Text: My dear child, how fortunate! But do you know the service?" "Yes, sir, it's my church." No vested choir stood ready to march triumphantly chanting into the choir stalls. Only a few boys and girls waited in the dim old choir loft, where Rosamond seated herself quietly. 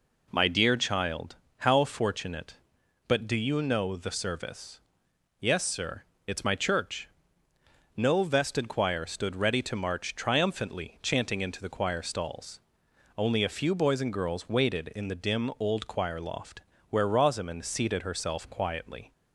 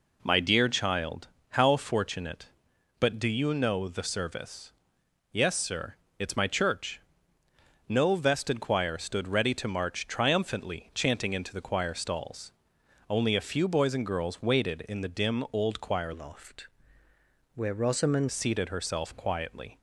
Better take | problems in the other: first | changes voice from "loft" to "Rosamond"; from 16.1 to 18.2 s; 2.1 s long

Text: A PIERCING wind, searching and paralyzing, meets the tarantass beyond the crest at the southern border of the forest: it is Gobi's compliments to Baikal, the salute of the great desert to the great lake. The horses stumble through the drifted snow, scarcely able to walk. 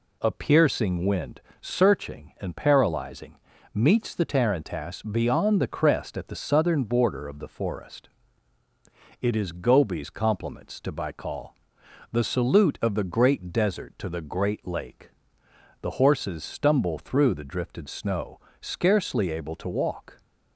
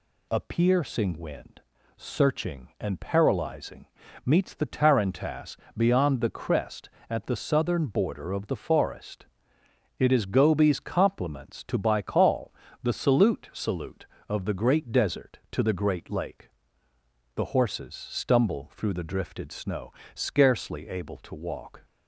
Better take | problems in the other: first | pauses between "tarantass" and "beyond"; slight; at 5.5 s; 0.22 s long // says "salute" twice; at 13.5 s

